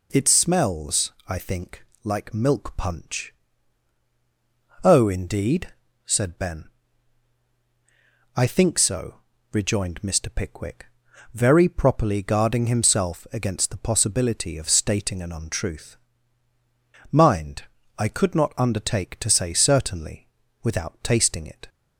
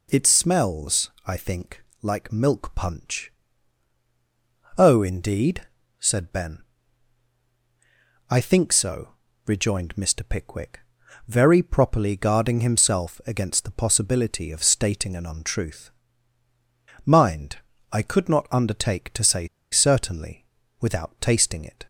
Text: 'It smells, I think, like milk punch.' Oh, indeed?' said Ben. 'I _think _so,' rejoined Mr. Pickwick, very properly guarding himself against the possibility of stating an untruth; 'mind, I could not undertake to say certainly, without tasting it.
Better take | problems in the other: first | pauses between "say" and "certainly"; slight; at 19.4 s; 0.24 s long

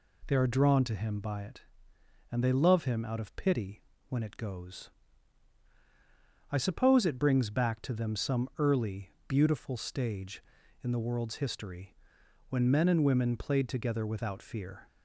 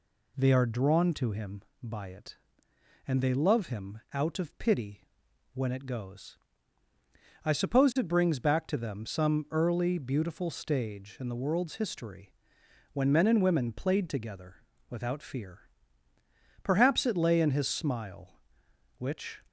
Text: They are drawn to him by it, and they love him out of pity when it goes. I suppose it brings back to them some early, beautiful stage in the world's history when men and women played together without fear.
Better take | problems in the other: first | pauses between "pity" and "when"; noticeable; at 5.0 s; 0.48 s long; slight in the first // pauses between "history" and "when"; noticeable; at 12.3 s; 0.60 s long; noticeable in the first // pauses between "together" and "without"; slight; at 14.5 s; 0.34 s long // goes on to say "Perhaps it lay in his smile which"; strong; from 16.6 s on; 2.7 s long

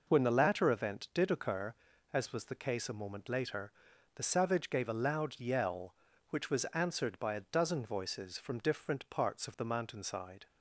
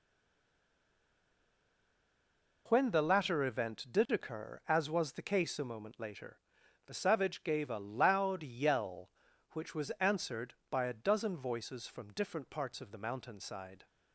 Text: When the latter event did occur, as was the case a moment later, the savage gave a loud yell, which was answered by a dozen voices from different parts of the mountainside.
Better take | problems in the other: first | stays silent before the first word; strong; until 2.6 s; 2.6 s long

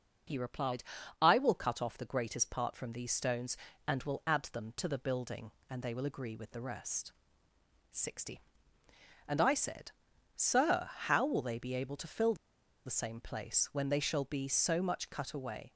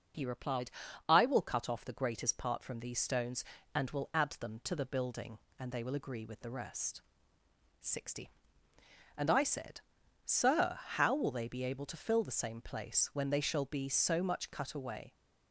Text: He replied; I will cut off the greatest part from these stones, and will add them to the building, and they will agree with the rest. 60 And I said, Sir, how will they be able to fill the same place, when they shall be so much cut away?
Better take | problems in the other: second | pauses between "fill" and "the"; noticeable; at 12.3 s; 0.51 s long

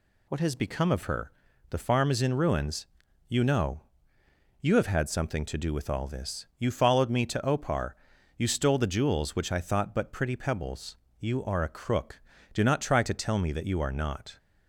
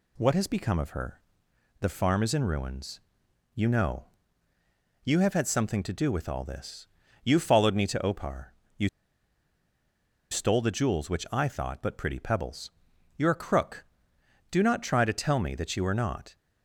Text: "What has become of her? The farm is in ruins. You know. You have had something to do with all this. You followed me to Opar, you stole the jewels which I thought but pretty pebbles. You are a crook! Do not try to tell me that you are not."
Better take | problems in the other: first | pauses between "you" and "stole"; strong; at 8.8 s; 1.4 s long

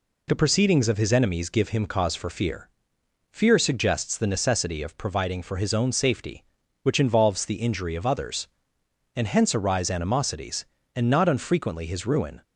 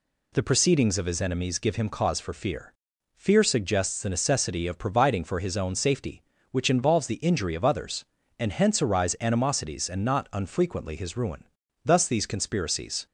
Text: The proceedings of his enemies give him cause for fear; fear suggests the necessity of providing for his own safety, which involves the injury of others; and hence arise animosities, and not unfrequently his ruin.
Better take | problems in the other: first | goes on to say "Thus these conspiracies"; noticeable; from 11.8 s on; 1.2 s long

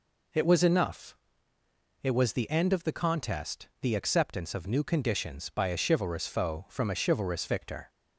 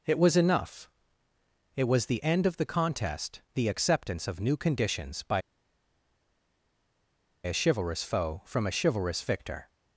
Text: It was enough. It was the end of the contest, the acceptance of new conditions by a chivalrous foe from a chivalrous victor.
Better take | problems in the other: first | pauses between "by" and "a"; strong; at 5.4 s; 2.0 s long

